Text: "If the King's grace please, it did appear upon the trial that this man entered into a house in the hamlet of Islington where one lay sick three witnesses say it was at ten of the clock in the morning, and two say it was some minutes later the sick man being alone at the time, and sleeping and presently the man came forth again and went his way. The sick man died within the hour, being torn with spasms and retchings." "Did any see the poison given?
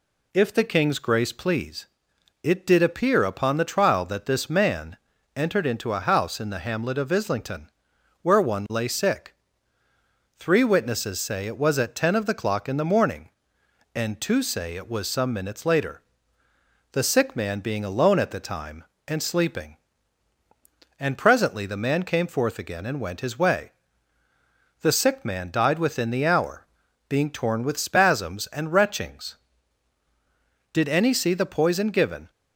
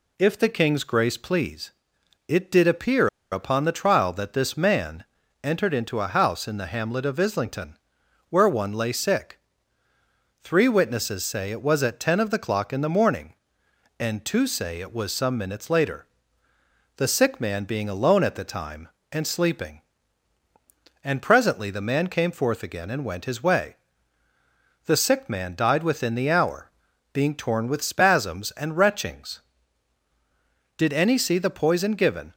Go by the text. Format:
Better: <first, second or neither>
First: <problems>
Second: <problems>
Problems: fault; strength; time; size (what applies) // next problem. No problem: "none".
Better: first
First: pauses between "man" and "entered"; at 4.9 s; 0.38 s long // pauses between "Islington" and "where"; noticeable; at 7.7 s; 0.50 s long // pauses between "sick" and "three"; at 9.3 s; 1.0 s long // pauses between "later" and "the"; noticeable; at 16.0 s; 0.90 s long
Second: pauses between "appear" and "upon"; slight; at 3.0 s; 0.24 s long // pauses between "man" and "entered"; at 5.0 s; 0.38 s long // pauses between "Islington" and "where"; noticeable; at 7.7 s; 0.50 s long // pauses between "sick" and "three"; at 9.3 s; 1.0 s long // pauses between "later" and "the"; noticeable; at 16.0 s; 0.90 s long